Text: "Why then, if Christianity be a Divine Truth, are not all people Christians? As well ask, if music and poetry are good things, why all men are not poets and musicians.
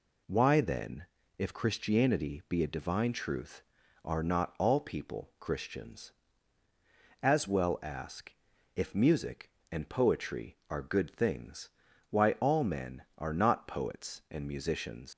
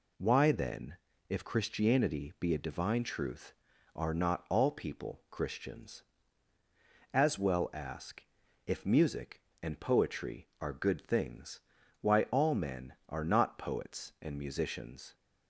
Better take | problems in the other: second | leaves "musicians" unfinished; at 15.1 s; 110 ms

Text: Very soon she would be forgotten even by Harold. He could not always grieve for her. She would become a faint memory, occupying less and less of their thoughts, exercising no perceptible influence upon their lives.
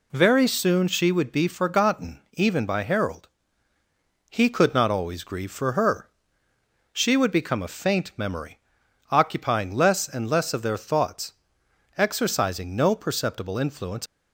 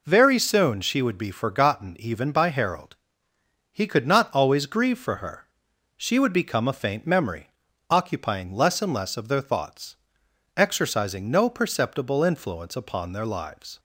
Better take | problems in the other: second | stops before "upon their lives"; at 14.0 s

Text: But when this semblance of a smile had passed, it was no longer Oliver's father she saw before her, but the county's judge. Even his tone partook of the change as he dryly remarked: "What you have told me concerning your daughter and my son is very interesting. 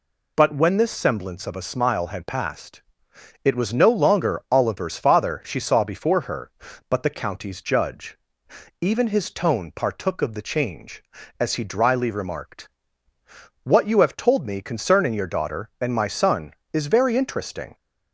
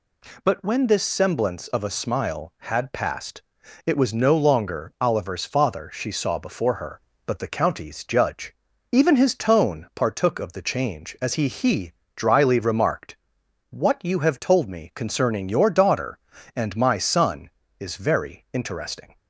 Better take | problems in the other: first | says "he" twice; at 11.4 s

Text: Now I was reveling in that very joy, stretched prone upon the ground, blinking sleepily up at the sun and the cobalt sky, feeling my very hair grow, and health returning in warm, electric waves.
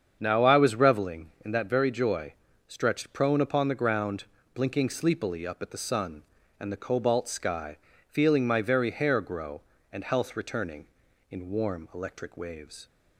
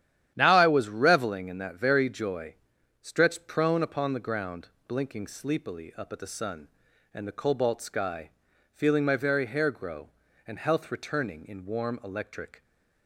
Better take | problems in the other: first | starts louder than the rest; strong; until 1.3 s; 10.5 dB; strong in the first // stops before "waves"; at 12.6 s

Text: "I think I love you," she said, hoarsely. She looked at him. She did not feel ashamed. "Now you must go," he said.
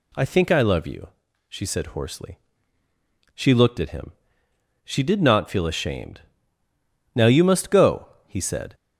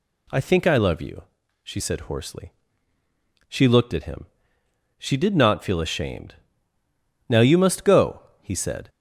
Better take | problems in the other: neither | none

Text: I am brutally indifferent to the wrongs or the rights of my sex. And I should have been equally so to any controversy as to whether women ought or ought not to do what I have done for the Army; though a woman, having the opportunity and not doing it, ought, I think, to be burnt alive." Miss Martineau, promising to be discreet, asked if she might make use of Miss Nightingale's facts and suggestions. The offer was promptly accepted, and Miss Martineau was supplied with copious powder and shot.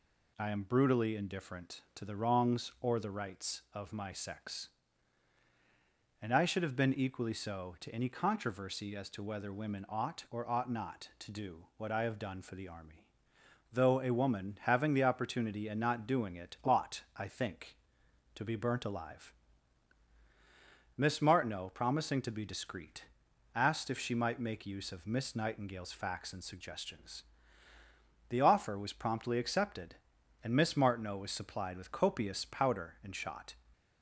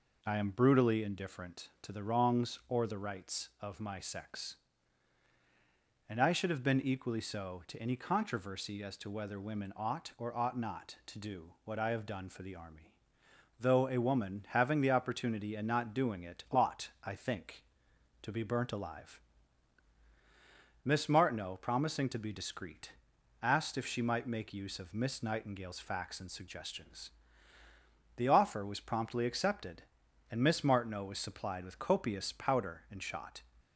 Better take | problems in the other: first | starts louder than the rest; noticeable; until 1.1 s; 4.5 dB

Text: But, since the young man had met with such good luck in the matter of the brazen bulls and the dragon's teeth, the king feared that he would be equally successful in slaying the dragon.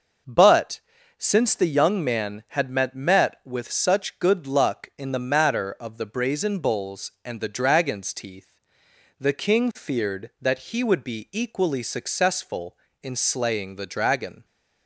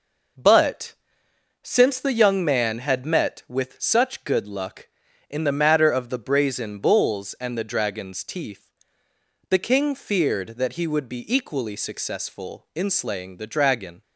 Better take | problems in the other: second | says "met" twice; at 2.9 s

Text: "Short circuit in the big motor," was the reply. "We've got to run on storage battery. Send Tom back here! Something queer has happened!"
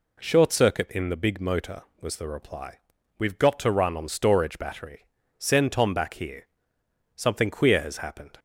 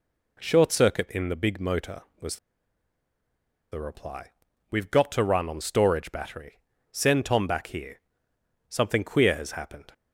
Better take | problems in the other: first | pauses between "was" and "the"; strong; at 2.3 s; 1.3 s long

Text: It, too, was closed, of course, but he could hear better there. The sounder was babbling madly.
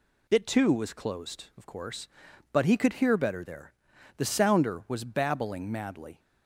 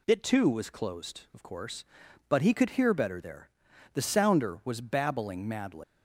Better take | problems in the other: first | leaves "madly" unfinished; at 5.8 s; 120 ms

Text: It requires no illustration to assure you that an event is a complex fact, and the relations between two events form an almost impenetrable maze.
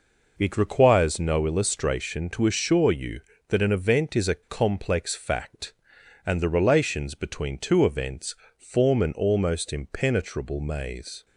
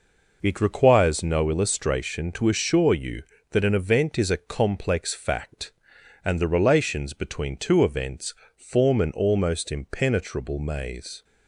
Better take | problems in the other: neither | pauses between "events" and "form"; slight; the same in both

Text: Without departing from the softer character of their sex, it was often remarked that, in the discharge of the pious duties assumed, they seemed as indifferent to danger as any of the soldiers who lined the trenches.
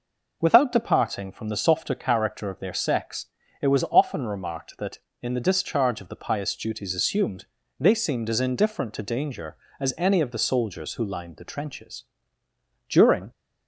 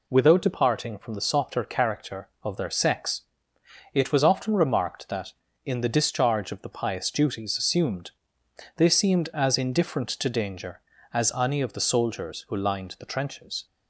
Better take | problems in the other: second | goes on to say "During"; slight; from 12.8 s on; 0.42 s long

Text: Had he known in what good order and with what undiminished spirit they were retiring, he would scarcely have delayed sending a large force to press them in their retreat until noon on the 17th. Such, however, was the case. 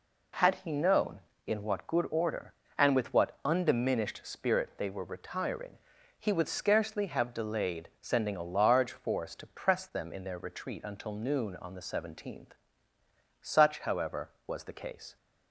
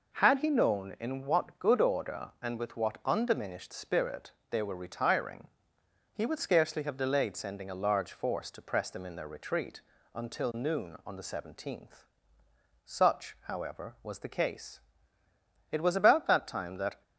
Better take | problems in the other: first | pauses between "spirit" and "they"; slight; at 4.3 s; 0.18 s long // pauses between "retreat" and "until"; slight; at 9.7 s; 0.34 s long // goes on to say "It was about that time that"; noticeable; from 15.7 s on; 1.3 s long

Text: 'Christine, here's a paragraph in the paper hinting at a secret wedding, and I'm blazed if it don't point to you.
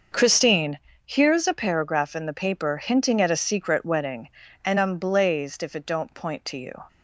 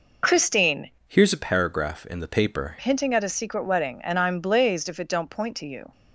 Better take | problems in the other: first | changes voice from "here's" to "paper"; from 1.0 to 2.7 s; 1.7 s long

